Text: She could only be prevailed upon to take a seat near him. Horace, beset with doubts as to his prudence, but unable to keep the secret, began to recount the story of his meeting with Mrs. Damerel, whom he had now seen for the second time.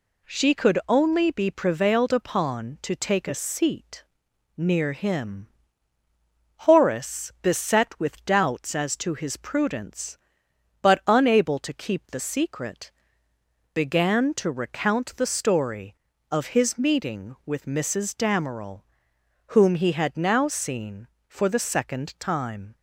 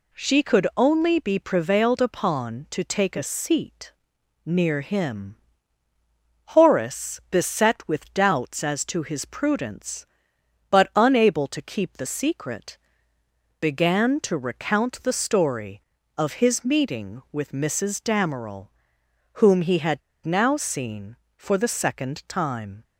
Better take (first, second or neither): first